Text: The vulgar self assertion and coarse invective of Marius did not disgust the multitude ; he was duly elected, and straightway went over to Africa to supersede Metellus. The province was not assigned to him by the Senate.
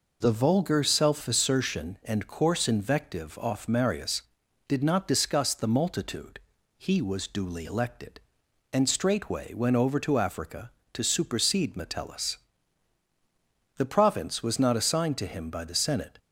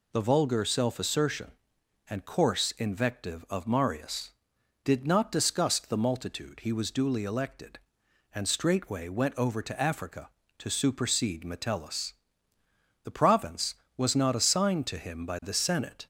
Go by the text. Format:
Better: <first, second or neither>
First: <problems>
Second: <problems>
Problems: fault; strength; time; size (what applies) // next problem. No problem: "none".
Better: second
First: says "off" for "of"; at 3.3 s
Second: none